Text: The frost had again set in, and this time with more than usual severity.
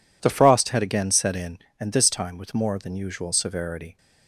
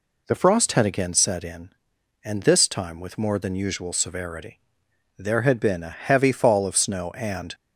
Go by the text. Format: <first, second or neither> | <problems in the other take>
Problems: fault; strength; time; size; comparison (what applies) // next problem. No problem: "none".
first | goes on to say "There had been a heavy fall of snow and"; strong; from 5.1 s on; 2.3 s long